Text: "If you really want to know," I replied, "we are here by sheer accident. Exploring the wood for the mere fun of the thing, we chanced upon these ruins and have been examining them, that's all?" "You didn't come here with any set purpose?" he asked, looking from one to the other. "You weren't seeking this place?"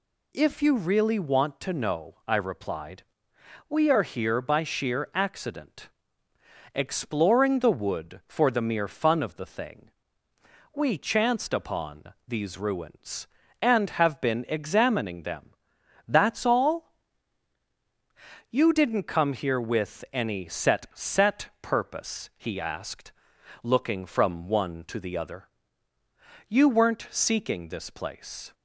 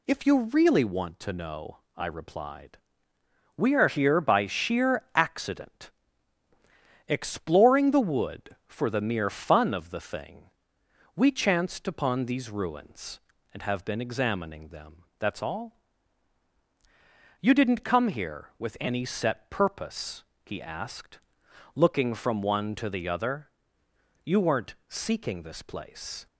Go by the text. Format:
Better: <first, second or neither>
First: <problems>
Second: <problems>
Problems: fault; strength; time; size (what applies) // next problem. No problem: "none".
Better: second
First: says "set" twice; at 20.9 s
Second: none